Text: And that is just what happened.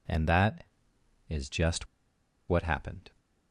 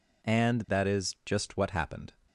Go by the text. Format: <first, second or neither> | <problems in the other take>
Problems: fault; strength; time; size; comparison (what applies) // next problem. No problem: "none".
second | pauses between "just" and "what"; noticeable; at 1.8 s; 0.62 s long